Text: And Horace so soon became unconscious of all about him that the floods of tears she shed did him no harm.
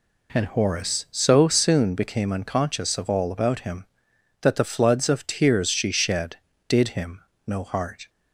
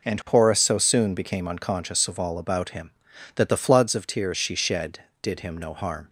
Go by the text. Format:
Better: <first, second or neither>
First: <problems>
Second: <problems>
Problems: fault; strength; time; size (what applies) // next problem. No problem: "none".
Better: second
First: pauses between "him" and "no"; slight; at 7.2 s; 0.26 s long // says "heart" for "harm"; at 7.6 s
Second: none